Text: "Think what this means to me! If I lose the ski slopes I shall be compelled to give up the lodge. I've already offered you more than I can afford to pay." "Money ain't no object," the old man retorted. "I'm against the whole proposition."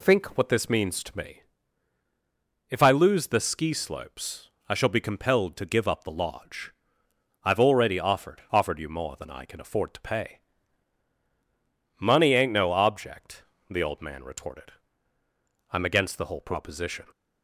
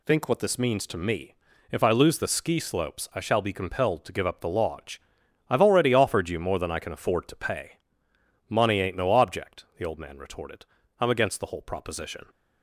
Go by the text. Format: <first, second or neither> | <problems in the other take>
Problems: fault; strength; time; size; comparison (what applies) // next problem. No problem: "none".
second | pauses between "slopes" and "I"; slight; at 4.4 s; 0.18 s long // says "offered" twice; at 8.5 s